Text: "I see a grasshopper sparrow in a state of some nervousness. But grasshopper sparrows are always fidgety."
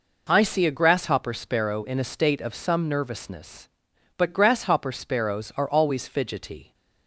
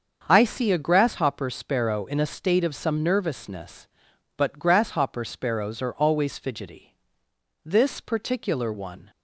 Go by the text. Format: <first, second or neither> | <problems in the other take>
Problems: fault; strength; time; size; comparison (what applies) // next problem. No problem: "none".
first | starts louder than the rest; until 1.2 s; 7 dB // goes on to say "This particular one"; from 7.6 s on; 1.4 s long